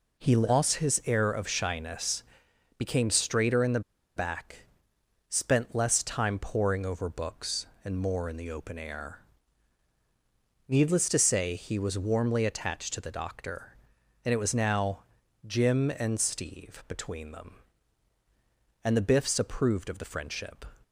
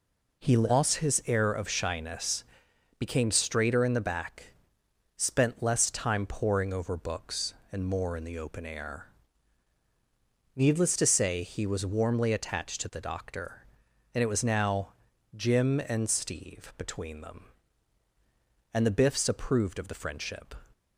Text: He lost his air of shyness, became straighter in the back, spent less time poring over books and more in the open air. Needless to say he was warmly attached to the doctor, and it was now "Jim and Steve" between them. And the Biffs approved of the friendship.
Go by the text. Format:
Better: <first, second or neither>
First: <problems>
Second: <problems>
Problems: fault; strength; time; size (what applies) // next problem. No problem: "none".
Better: second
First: pauses between "the" and "back"; slight; at 3.8 s; 0.36 s long // pauses between "now" and "Jim"; at 15.0 s; 0.42 s long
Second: pauses between "now" and "Jim"; at 14.9 s; 0.42 s long